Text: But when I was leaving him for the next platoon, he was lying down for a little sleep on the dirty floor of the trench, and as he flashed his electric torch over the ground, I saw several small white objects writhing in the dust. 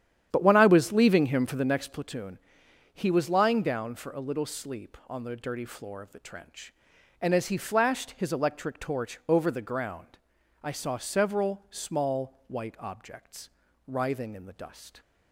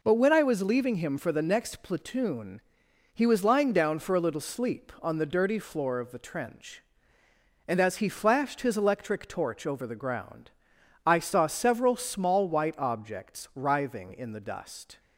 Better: second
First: starts louder than the rest; strong; until 2.0 s; 10 dB // pauses between "objects" and "writhing"; at 13.4 s; 0.38 s long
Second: none

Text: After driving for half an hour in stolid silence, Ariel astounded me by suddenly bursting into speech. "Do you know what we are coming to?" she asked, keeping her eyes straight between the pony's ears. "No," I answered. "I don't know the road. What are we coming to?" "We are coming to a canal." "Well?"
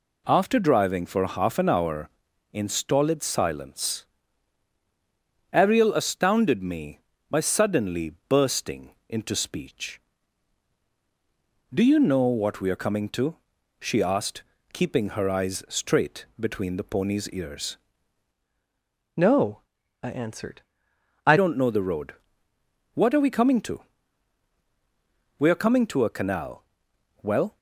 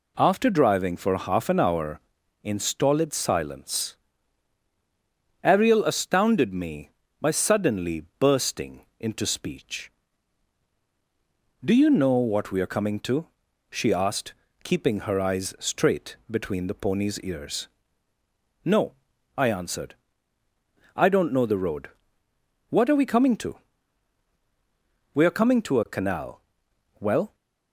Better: second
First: changes voice from "No" to "I"; from 19.1 to 21.3 s; 2.2 s long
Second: none

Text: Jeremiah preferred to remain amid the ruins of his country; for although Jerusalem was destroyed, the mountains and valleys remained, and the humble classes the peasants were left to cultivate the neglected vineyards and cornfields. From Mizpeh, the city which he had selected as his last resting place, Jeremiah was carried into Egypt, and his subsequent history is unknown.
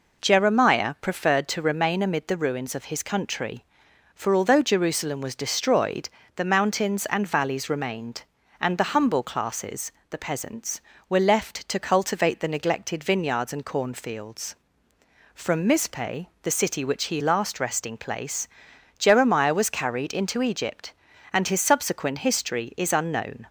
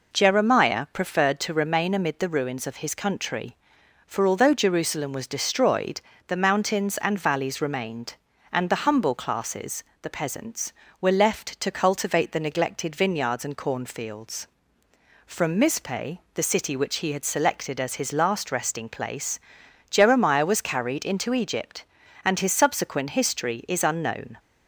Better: second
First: pauses between "classes" and "the"; slight; at 9.9 s; 0.18 s long // skips "had selected as his"; at 17.2 s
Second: pauses between "classes" and "the"; slight; at 9.8 s; 0.18 s long

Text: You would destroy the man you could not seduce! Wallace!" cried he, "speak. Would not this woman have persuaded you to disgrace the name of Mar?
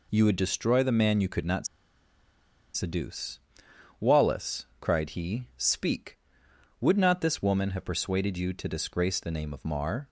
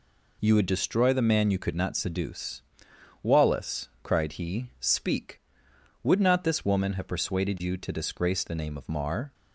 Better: second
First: pauses between "not" and "seduce"; at 1.6 s; 1.0 s long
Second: none

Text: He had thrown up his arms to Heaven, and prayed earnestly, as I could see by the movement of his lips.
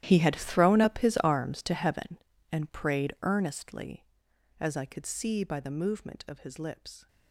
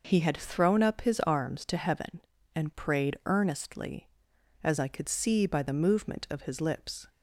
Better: second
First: gets quieter; strong; throughout; 16 dB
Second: none

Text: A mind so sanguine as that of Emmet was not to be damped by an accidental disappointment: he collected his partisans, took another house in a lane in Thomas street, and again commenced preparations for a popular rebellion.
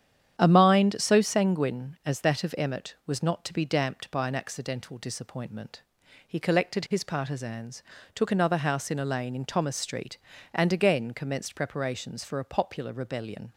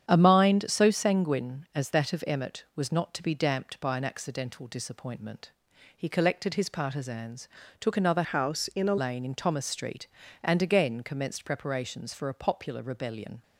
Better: first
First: starts louder than the rest; strong; until 1.4 s; 9.5 dB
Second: starts louder than the rest; strong; until 1.1 s; 9 dB // changes voice from "house" to "a"; from 8.2 to 8.9 s; 0.7 s long

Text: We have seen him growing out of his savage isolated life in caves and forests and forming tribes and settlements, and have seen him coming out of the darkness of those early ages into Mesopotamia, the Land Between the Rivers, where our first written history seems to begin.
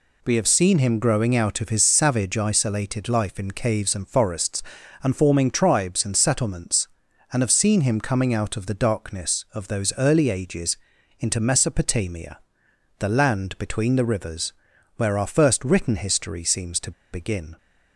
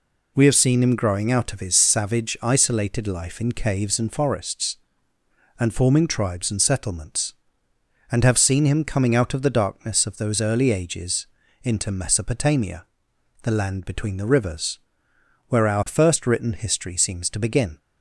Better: second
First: pauses between "ages" and "into"; at 10.7 s; 0.42 s long // pauses between "to" and "begin"; slight; at 16.9 s; 0.21 s long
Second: pauses between "ages" and "into"; slight; at 11.2 s; 0.36 s long

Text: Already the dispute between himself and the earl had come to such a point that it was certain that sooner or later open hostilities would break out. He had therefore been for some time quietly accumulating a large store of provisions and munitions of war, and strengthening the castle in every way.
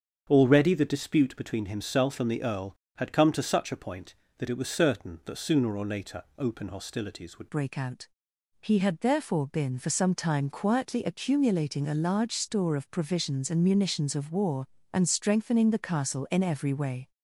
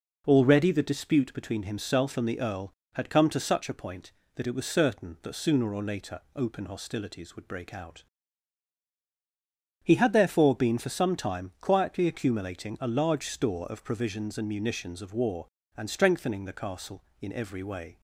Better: second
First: starts louder than the rest; until 1.3 s; 7 dB // pauses between "later" and "open"; slight; at 6.2 s; 0.16 s long // changes voice at "break"; from 7.5 s on; 9.6 s long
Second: pauses between "later" and "open"; slight; at 6.1 s; 0.16 s long

